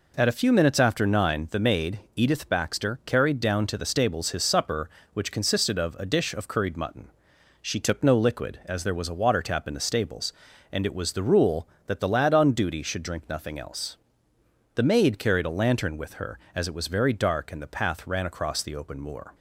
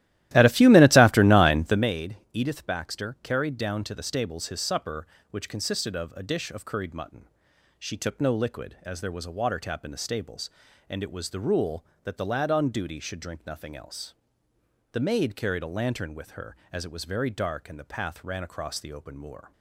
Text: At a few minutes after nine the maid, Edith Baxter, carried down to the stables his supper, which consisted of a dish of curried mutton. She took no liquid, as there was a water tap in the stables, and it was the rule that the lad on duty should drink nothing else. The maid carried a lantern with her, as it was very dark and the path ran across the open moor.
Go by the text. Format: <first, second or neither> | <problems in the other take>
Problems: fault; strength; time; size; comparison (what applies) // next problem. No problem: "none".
first | starts louder than the rest; strong; until 1.9 s; 15 dB